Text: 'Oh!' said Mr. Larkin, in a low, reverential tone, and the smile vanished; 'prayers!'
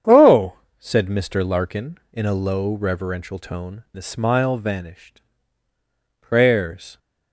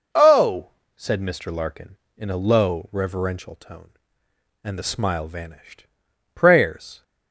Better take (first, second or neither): second